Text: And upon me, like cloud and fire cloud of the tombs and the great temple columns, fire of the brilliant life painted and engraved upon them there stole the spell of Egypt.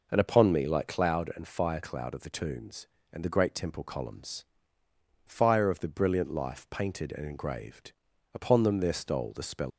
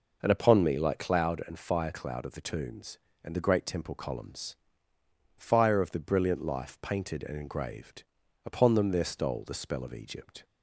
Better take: second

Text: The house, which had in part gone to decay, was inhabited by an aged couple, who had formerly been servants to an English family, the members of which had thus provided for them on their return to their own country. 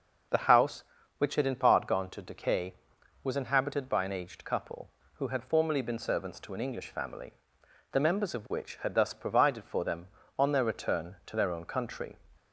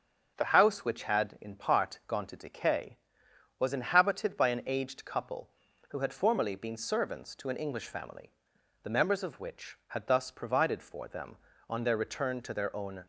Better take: first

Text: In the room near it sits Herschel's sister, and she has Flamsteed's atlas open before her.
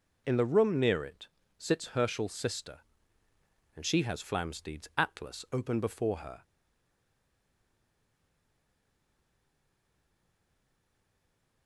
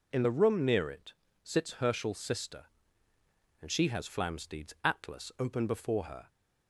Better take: second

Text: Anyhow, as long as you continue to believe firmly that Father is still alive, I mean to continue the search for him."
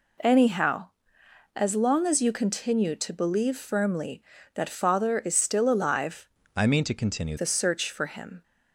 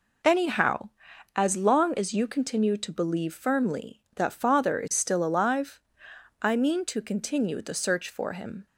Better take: second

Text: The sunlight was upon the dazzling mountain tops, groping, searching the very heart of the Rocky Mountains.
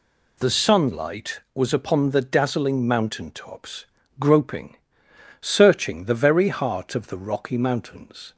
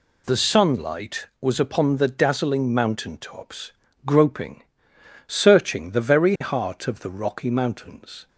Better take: neither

